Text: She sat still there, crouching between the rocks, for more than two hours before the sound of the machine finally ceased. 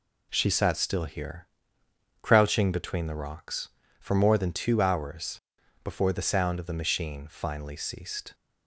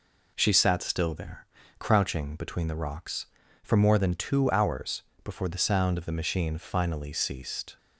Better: second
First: says "here" for "there"; at 1.0 s // pauses between "hours" and "before"; at 5.4 s; 0.42 s long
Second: pauses between "hours" and "before"; slight; at 5.0 s; 0.20 s long

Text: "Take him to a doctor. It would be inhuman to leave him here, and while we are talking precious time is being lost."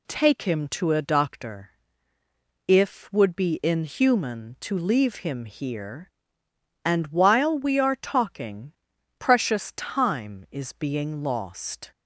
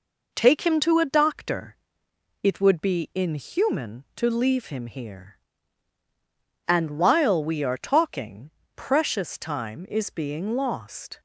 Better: second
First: says "If" for "It"; at 2.6 s // pauses between "talking" and "precious"; at 8.7 s; 0.44 s long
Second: pauses between "talking" and "precious"; slight; at 8.5 s; 0.24 s long

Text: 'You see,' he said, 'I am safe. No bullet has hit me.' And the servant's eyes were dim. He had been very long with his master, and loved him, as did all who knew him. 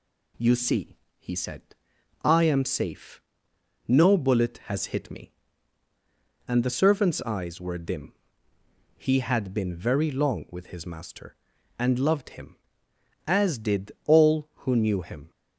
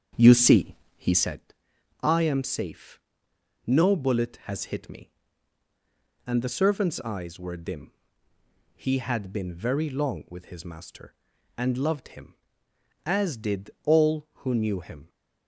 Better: first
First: none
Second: starts louder than the rest; strong; until 1.4 s; 7.5 dB

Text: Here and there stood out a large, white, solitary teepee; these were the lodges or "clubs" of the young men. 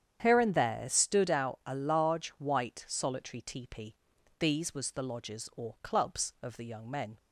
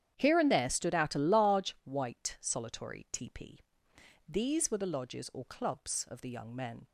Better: second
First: starts louder than the rest; strong; until 1.2 s; 9 dB // says "was" for "were"; at 4.7 s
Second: starts louder than the rest; strong; until 1.1 s; 9.5 dB

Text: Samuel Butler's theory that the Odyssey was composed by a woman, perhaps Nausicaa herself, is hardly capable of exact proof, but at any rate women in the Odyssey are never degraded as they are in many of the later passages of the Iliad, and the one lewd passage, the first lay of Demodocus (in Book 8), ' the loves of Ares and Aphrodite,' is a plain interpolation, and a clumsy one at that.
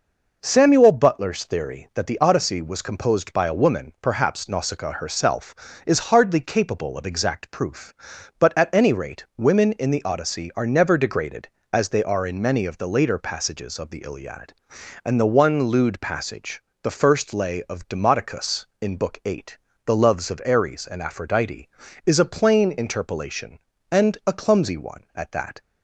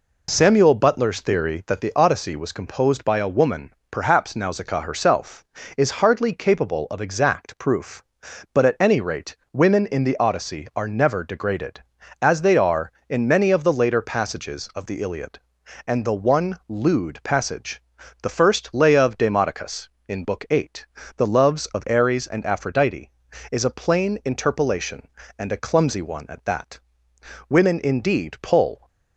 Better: first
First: none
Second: pauses between "rate" and "women"; slight; at 9.3 s; 0.18 s long // goes on to say "Women indeed pull"; from 27.4 s on; 1.3 s long

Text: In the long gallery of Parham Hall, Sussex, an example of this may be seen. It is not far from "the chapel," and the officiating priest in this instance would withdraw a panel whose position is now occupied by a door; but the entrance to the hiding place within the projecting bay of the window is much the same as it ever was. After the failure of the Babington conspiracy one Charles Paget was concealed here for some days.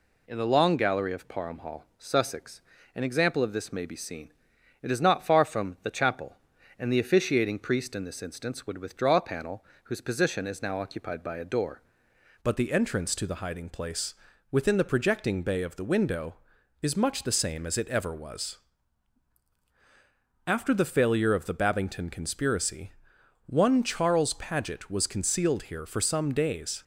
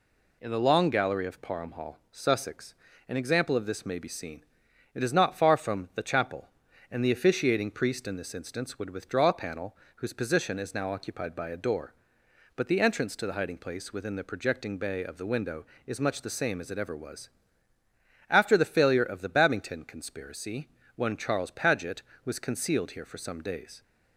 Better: second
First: pauses between "panel" and "whose"; slight; at 9.6 s; 0.20 s long // changes voice at "but"; from 12.4 s on; 14.4 s long // pauses between "place" and "within"; at 14.1 s; 0.38 s long // pauses between "conspiracy" and "one"; noticeable; at 22.9 s; 0.56 s long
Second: pauses between "panel" and "whose"; slight; at 9.7 s; 0.20 s long // pauses between "conspiracy" and "one"; slight; at 20.6 s; 0.26 s long

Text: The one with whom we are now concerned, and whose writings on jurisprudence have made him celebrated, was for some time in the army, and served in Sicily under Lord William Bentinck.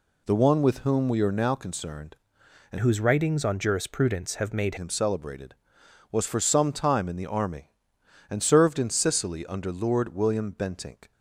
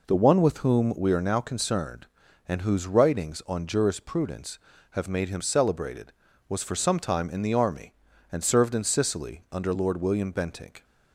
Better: second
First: changes voice from "whose" to "made"; from 2.7 to 4.7 s; 2.0 s long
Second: none

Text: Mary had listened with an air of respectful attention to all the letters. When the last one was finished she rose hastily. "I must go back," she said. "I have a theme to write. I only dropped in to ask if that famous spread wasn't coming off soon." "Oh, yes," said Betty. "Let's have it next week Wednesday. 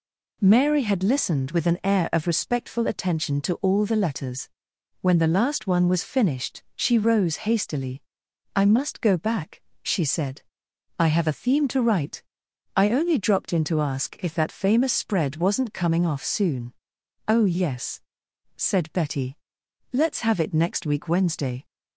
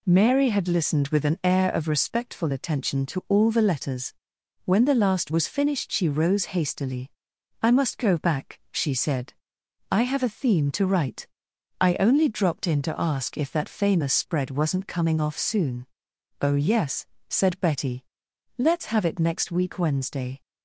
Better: first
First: none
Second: skips "one"; at 5.3 s

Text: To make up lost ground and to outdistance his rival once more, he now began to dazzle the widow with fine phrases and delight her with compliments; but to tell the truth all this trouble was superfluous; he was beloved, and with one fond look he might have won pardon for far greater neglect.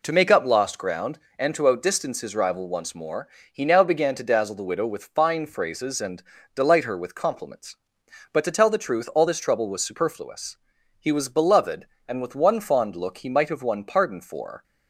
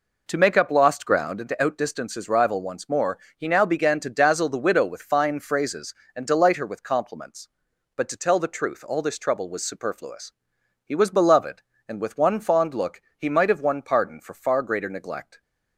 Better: second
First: pauses between "and" and "delight"; slight; at 6.2 s; 0.32 s long // stops before "far greater neglect"; at 14.6 s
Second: none

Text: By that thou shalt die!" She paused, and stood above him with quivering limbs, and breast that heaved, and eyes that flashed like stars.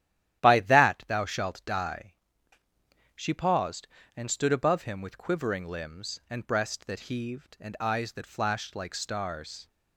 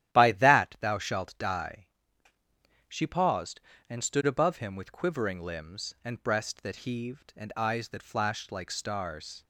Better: neither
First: starts louder than the rest; strong; until 1.4 s; 12.5 dB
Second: starts louder than the rest; strong; until 1.1 s; 12.5 dB

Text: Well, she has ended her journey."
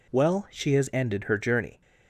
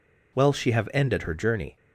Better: first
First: none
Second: says "have" for "has"; at 0.7 s

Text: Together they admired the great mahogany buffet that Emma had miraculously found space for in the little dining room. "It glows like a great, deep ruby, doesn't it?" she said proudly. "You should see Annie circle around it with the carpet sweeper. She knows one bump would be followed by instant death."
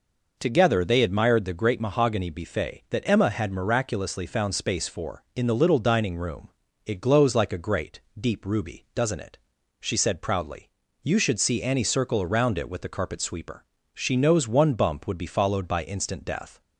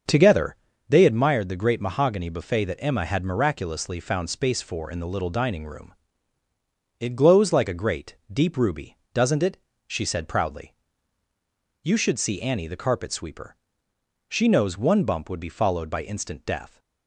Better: first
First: none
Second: starts louder than the rest; until 1.4 s; 6.5 dB // pauses between "Together" and "they"; slight; at 0.5 s; 0.34 s long // skips "circle around it with"; at 12.6 s

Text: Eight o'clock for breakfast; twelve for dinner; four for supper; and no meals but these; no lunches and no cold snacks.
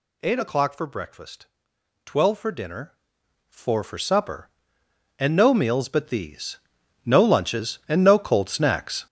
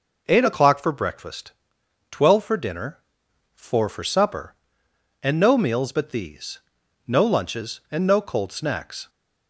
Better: second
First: gets louder; strong; throughout; 9 dB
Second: none

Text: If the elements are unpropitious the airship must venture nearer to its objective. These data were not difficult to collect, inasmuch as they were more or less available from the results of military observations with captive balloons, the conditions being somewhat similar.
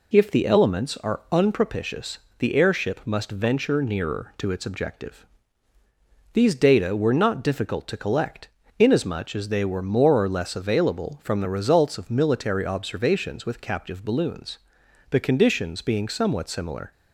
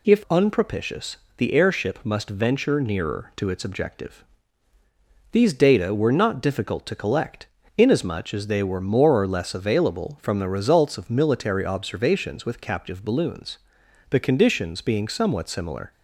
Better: first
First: pauses between "unpropitious" and "the"; slight; at 2.1 s; 0.20 s long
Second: skips "the elements are"; at 0.2 s // pauses between "unpropitious" and "the"; slight; at 1.1 s; 0.20 s long

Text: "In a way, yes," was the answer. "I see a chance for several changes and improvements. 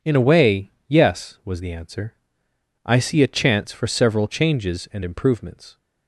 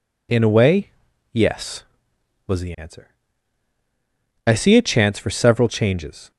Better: first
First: none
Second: stops before "and improvements"; at 6.3 s

